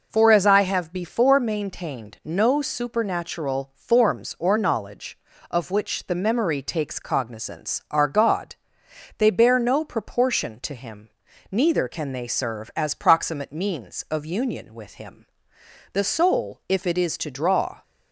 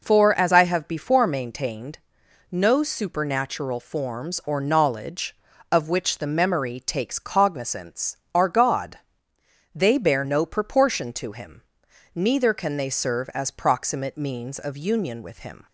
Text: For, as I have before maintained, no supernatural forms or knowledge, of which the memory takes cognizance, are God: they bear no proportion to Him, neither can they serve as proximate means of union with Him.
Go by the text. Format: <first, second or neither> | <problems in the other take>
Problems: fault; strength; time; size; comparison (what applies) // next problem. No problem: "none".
second | goes on to say "The soul if it is to draw"; strong; from 15.9 s on; 1.9 s long